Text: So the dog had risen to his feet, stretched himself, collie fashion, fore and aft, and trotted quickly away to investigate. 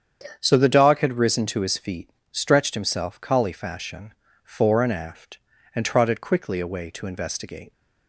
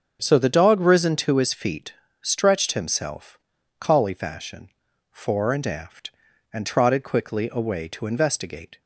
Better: first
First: starts louder than the rest; strong; until 1.4 s; 8 dB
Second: starts louder than the rest; until 1.2 s; 6.5 dB // skips "had"; at 0.8 s

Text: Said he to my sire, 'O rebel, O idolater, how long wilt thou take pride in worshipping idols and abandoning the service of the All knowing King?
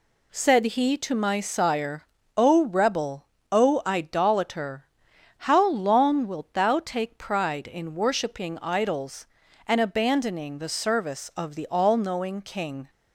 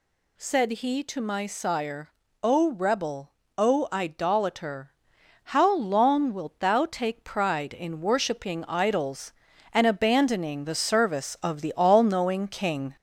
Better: first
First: none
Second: gets louder; slight; throughout; 3 dB

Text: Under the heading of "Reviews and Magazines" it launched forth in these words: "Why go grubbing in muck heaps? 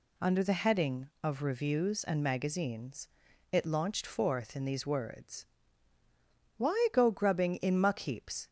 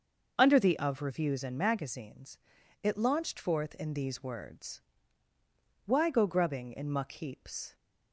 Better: first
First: pauses between "Magazines" and "it"; noticeable; at 3.0 s; 0.46 s long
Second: starts louder than the rest; noticeable; until 1.3 s; 6 dB // skips "heading"; at 0.7 s // pauses between "Magazines" and "it"; at 2.3 s; 0.42 s long

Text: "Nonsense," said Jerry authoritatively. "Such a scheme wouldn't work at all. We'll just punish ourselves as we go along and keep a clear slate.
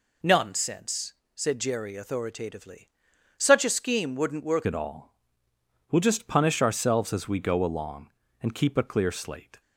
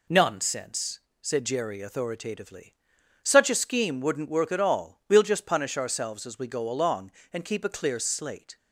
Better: second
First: changes voice at "at"; from 4.6 s on; 5.0 s long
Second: none

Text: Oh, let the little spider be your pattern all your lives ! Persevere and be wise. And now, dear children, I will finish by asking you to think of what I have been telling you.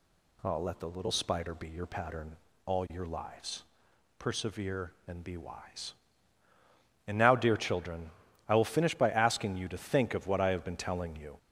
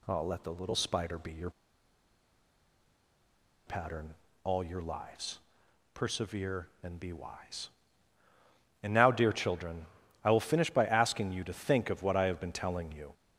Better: first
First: pauses between "pattern" and "all"; slight; at 2.3 s; 0.28 s long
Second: pauses between "your" and "pattern"; strong; at 1.4 s; 2.1 s long // pauses between "pattern" and "all"; slight; at 4.1 s; 0.28 s long

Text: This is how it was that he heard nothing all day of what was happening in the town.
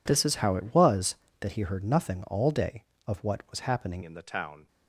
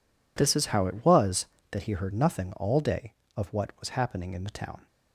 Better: second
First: changes voice at "in"; from 4.0 s on; 0.6 s long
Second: none

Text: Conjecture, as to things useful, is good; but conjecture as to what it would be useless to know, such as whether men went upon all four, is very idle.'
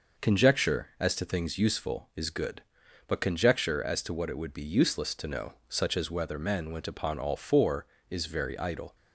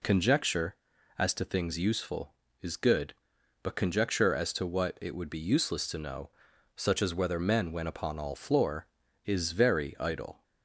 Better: first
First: none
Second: says "floor" for "four"; at 8.3 s

